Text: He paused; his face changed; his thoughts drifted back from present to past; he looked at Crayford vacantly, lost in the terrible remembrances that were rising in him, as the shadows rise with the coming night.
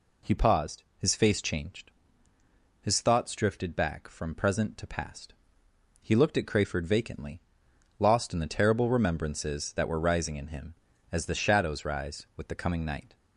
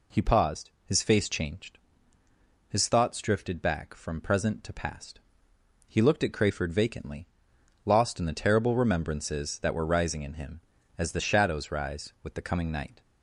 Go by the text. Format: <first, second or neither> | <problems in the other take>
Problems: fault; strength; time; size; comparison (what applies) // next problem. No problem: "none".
neither | none